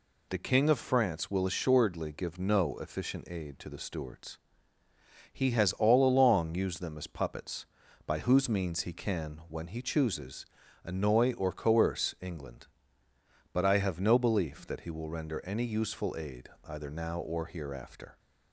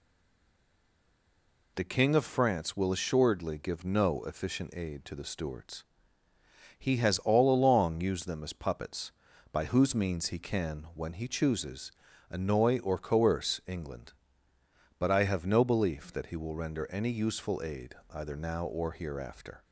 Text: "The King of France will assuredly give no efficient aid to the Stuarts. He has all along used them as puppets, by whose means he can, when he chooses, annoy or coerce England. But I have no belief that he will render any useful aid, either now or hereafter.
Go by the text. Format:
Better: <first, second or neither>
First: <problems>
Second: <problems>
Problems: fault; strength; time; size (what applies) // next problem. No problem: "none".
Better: first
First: none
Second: stays silent before the first word; noticeable; until 1.7 s; 1.7 s long